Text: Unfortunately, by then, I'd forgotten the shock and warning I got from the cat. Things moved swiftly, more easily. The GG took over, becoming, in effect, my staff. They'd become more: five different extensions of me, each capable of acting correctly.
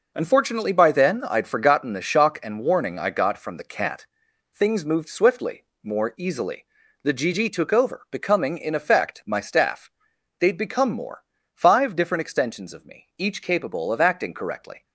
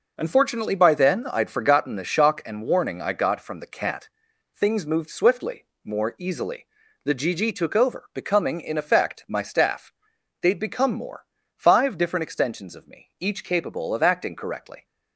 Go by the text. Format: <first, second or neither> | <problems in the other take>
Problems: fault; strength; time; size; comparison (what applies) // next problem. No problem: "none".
neither | none